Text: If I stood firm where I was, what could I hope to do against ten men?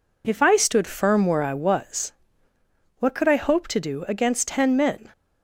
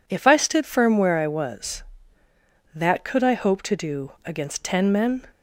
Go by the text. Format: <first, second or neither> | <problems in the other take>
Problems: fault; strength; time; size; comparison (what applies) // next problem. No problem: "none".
first | says "that" for "what"; at 2.7 s